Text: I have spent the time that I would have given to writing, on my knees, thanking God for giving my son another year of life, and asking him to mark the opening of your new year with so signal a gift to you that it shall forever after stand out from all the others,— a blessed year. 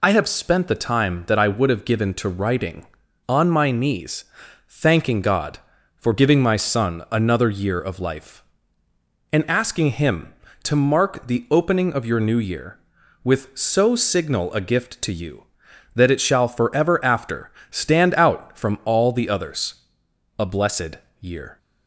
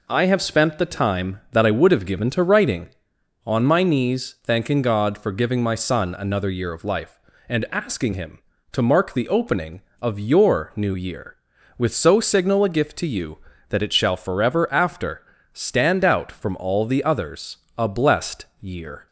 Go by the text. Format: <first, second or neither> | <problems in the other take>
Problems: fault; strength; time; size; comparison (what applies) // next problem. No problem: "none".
neither | pauses between "after" and "stand"; slight; the same in both // pauses between "blessed" and "year"; slight; the same in both